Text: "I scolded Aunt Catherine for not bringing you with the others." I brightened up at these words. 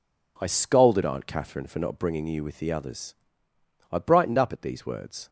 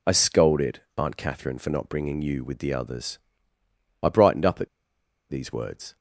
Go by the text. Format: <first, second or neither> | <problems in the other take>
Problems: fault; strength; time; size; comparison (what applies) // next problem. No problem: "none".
first | pauses between "scolded" and "Aunt"; slight; at 0.8 s; 0.16 s long // pauses between "at" and "these"; noticeable; at 4.6 s; 0.63 s long